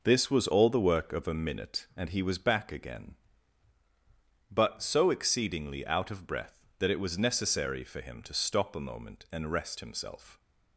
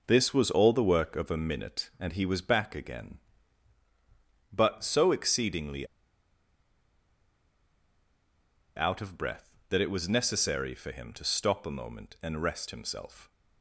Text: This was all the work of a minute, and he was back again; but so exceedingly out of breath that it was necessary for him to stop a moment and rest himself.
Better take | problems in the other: first | pauses between "exceedingly" and "out"; strong; at 5.8 s; 2.9 s long

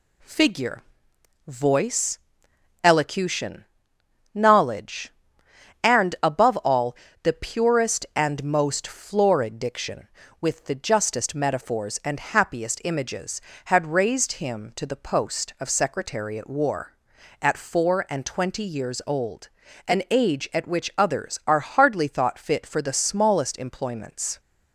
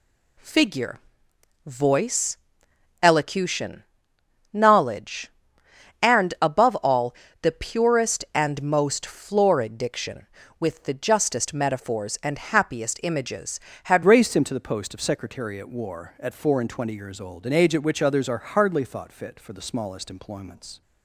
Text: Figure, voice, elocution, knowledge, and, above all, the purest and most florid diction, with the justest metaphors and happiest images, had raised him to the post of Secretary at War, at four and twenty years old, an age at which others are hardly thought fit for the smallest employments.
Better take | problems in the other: first | changes voice at "raised"; from 14.0 s on; 6.8 s long

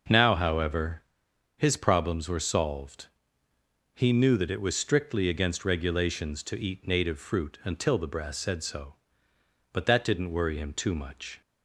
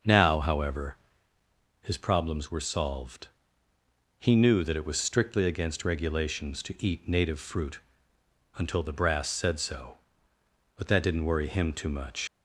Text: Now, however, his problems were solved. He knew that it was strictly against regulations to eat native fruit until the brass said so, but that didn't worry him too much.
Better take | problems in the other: first | starts louder than the rest; noticeable; until 1.9 s; 6 dB // pauses between "fruit" and "until"; noticeable; at 7.7 s; 0.78 s long // leaves "much" unfinished; at 12.2 s; 80 ms

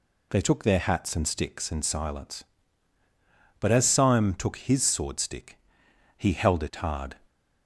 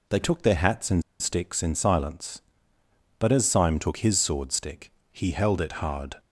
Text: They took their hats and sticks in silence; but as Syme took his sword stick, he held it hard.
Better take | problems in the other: first | pauses between "and" and "sticks"; slight; at 1.0 s; 0.18 s long

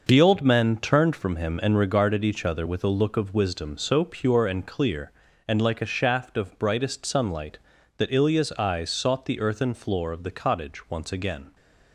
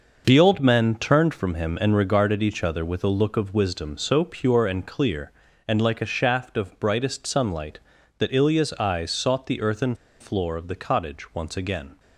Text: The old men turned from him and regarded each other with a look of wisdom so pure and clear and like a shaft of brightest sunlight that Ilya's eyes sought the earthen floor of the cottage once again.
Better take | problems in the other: first | starts louder than the rest; noticeable; until 1.2 s; 6 dB; noticeable in the first // pauses between "earthen" and "floor"; slight; at 9.9 s; 0.26 s long

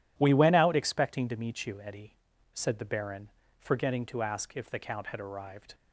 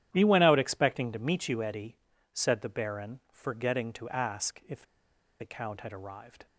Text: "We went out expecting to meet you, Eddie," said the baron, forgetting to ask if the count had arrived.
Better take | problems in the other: first | starts louder than the rest; strong; until 1.1 s; 11 dB // pauses between "if" and "the"; noticeable; at 4.8 s; 0.57 s long

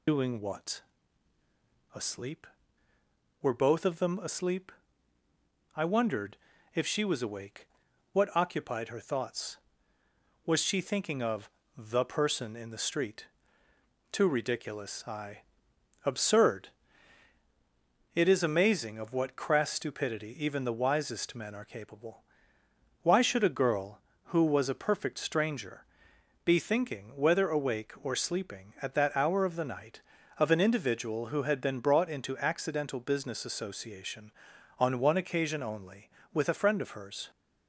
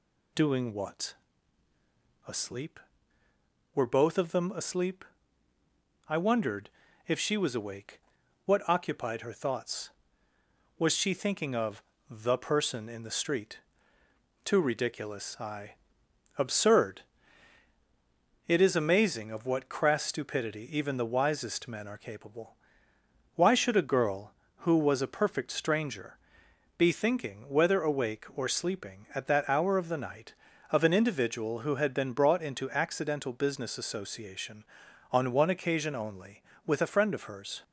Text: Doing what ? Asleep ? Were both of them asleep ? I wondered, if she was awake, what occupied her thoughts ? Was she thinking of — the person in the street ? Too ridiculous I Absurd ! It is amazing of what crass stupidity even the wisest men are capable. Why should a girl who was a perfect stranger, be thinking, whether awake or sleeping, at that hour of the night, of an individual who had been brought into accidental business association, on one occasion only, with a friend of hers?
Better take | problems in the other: second | loses the start of "Doing"; at 0.0 s; 55 ms // pauses between "I" and "Absurd"; noticeable; at 15.4 s; 0.66 s long; noticeable in the second

